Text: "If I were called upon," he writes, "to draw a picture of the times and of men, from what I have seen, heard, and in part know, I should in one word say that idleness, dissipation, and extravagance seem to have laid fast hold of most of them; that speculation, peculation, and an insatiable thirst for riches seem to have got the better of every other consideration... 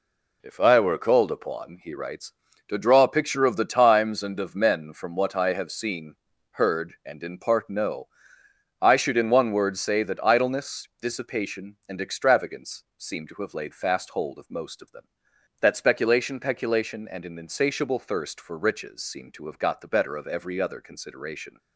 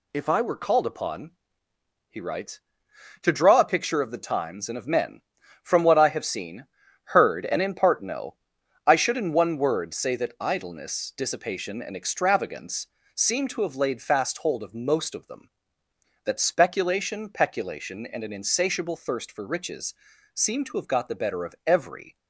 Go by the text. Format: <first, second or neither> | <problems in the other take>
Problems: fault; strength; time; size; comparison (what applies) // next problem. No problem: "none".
first | pauses between "extravagance" and "seem"; slight; at 12.8 s; 0.26 s long // pauses between "riches" and "seem"; at 19.9 s; 0.40 s long // stops before "other consideration"; at 22.1 s